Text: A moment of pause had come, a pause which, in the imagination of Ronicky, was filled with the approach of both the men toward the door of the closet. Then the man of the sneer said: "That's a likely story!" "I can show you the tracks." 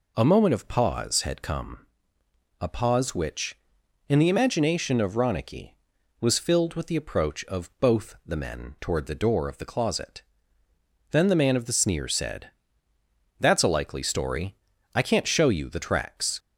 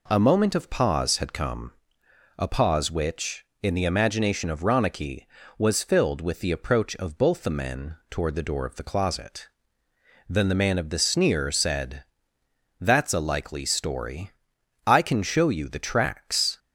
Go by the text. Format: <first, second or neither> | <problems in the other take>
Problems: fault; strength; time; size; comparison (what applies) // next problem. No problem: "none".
second | says "can't" for "can"; at 15.0 s